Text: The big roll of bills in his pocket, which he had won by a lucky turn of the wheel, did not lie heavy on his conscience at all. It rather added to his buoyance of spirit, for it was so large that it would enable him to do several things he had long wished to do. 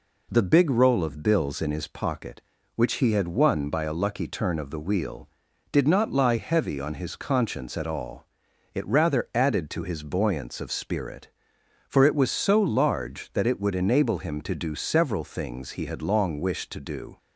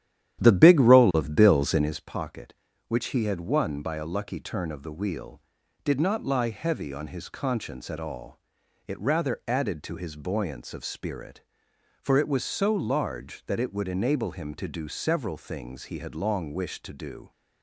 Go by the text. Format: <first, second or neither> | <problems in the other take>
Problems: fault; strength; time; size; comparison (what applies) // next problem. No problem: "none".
first | starts louder than the rest; strong; until 2.0 s; 11.5 dB